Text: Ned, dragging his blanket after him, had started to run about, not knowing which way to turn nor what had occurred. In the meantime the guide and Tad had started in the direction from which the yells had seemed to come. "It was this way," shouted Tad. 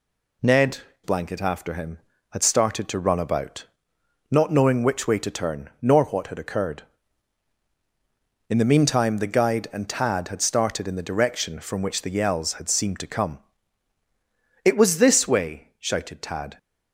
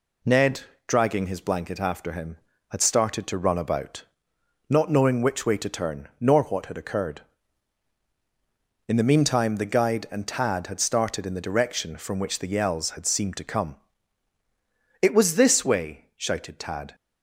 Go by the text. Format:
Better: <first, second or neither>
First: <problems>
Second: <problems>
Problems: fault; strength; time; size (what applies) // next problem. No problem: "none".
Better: second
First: skips "dragging his"; at 0.9 s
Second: none